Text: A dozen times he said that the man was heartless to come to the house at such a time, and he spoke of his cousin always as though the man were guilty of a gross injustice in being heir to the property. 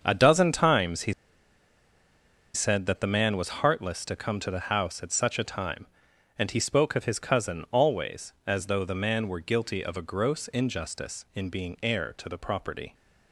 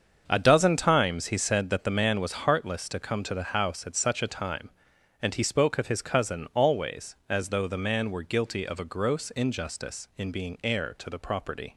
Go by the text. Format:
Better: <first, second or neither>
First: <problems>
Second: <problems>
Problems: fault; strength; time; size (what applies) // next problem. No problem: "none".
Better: second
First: starts louder than the rest; until 1.0 s; 7 dB // pauses between "he" and "said"; strong; at 1.1 s; 1.4 s long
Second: starts louder than the rest; until 1.2 s; 7 dB